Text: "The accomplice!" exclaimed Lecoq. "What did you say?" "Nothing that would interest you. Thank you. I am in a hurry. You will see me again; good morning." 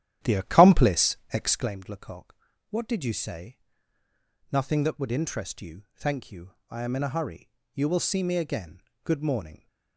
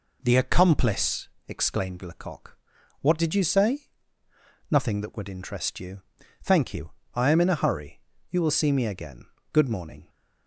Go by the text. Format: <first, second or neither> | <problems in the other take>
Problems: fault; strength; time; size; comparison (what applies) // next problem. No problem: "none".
second | starts louder than the rest; strong; until 1.7 s; 11.5 dB